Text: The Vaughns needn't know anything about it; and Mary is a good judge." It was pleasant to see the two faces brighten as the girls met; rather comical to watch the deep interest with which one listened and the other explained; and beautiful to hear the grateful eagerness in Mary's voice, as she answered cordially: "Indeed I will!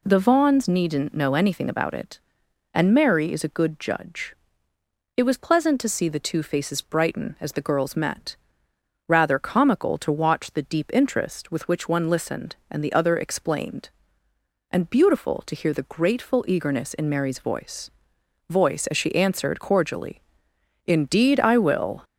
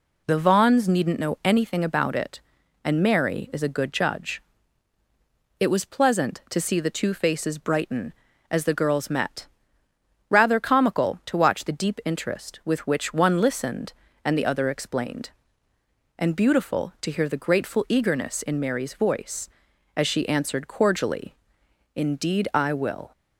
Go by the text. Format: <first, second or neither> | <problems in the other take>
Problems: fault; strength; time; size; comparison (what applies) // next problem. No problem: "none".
second | says "voice" twice; at 18.4 s